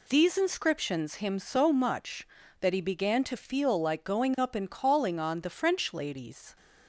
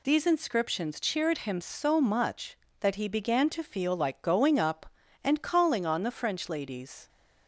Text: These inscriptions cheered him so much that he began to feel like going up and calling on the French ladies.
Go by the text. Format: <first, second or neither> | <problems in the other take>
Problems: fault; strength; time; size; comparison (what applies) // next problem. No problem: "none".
second | skips "cheered"; at 1.1 s